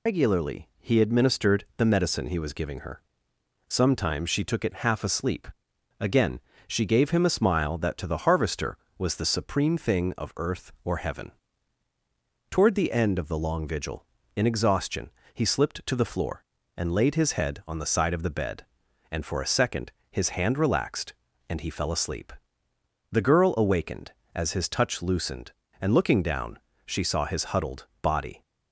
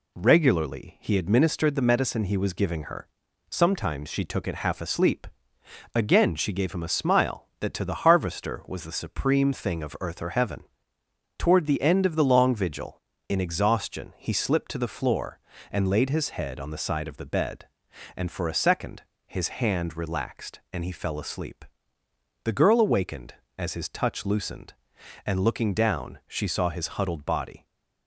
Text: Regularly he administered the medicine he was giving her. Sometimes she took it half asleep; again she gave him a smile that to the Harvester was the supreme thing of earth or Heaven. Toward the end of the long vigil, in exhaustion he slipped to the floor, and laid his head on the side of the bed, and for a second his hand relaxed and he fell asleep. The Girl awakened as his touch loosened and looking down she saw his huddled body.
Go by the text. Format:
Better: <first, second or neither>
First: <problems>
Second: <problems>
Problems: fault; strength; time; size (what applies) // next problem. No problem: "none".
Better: second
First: loses the start of "Regularly"; at 0.0 s; 105 ms // pauses between "again" and "she"; slight; at 6.4 s; 0.26 s long // pauses between "exhaustion" and "he"; slight; at 15.1 s; 0.22 s long // pauses between "second" and "his"; slight; at 19.9 s; 0.18 s long // pauses between "down" and "she"; slight; at 26.5 s; 0.26 s long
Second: pauses between "second" and "his"; slight; at 19.0 s; 0.24 s long